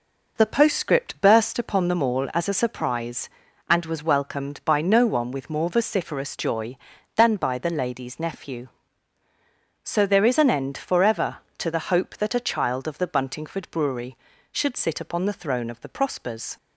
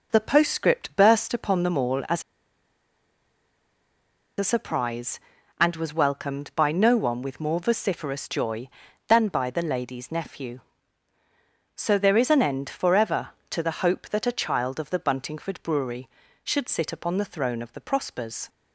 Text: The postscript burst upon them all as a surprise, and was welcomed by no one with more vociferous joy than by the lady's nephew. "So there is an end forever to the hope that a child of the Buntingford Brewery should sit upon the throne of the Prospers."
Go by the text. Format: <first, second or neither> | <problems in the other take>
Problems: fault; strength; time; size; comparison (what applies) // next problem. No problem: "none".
first | pauses between "as" and "a"; strong; at 2.2 s; 2.1 s long